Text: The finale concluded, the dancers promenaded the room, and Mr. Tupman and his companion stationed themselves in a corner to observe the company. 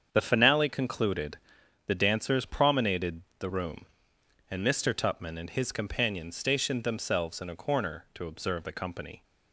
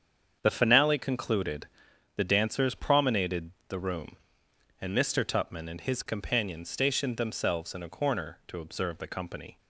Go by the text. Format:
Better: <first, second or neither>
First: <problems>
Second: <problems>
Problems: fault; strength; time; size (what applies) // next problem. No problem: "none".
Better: neither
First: starts louder than the rest; strong; until 1.1 s; 7.5 dB // pauses between "promenaded" and "the"; slight; at 3.2 s; 0.16 s long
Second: starts louder than the rest; strong; until 1.4 s; 7.5 dB // pauses between "promenaded" and "the"; slight; at 3.5 s; 0.16 s long